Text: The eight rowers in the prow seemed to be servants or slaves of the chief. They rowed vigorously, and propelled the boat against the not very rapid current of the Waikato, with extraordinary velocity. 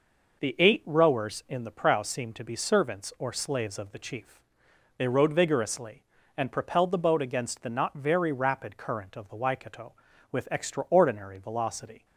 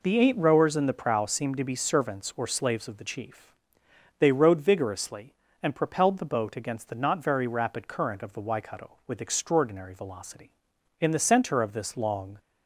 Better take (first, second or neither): first